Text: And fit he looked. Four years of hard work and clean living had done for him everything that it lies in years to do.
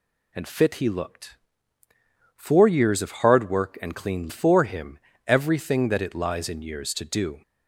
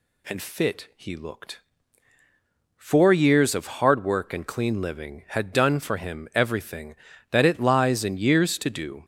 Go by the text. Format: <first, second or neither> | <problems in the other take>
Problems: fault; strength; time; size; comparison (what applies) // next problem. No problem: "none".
second | skips "living had done"; at 4.2 s // pauses between "him" and "everything"; slight; at 4.9 s; 0.28 s long